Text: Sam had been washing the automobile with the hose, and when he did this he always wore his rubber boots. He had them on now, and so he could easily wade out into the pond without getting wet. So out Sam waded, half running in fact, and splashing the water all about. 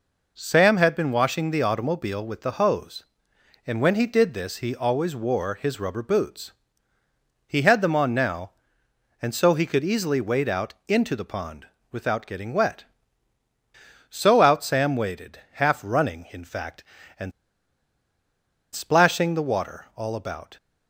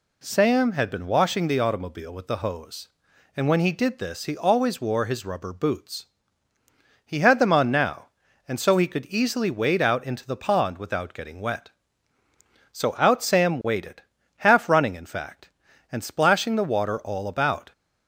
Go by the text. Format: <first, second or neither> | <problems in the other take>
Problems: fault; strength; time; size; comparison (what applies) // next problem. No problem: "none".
second | pauses between "pond" and "without"; slight; at 11.6 s; 0.22 s long // pauses between "and" and "splashing"; strong; at 17.3 s; 1.4 s long